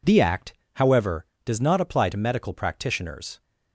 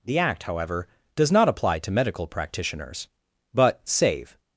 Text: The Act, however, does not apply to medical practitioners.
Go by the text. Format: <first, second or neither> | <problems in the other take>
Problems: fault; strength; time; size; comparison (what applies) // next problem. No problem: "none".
first | goes on to say "But save"; noticeable; from 3.5 s on; 0.86 s long